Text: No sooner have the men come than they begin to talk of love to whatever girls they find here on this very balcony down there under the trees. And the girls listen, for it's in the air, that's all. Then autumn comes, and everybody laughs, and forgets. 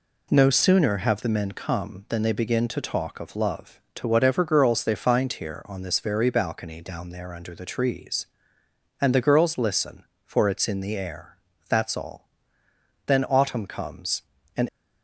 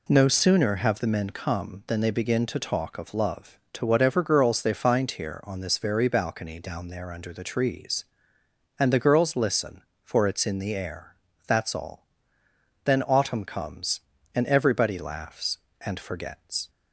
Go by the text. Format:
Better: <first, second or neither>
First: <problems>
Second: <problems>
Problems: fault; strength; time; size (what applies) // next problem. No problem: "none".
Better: second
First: stops before "everybody laughs and forgets"; at 14.6 s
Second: none